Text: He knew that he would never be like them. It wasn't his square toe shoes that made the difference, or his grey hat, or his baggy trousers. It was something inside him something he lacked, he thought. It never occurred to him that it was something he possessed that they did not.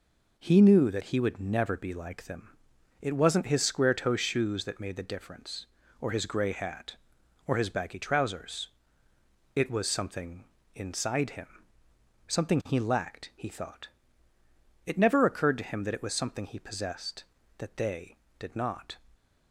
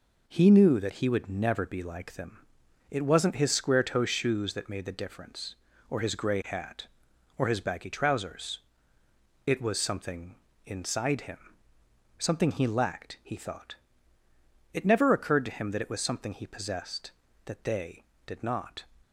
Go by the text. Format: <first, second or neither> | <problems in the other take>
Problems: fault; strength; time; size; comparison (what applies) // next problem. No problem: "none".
neither | pauses between "something" and "inside"; slight; the same in both // pauses between "him" and "something"; noticeable; the same in both